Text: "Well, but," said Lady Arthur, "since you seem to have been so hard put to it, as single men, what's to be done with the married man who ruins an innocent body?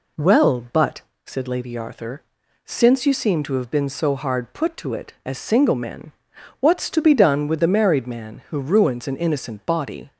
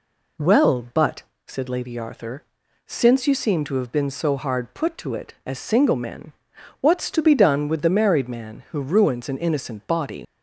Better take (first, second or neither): first